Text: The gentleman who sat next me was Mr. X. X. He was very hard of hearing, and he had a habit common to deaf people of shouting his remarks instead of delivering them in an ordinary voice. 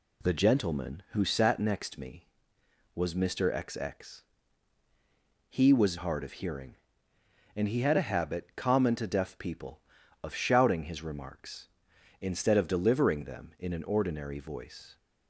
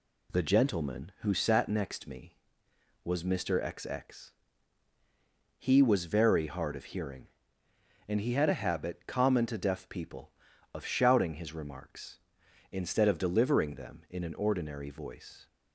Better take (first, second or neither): second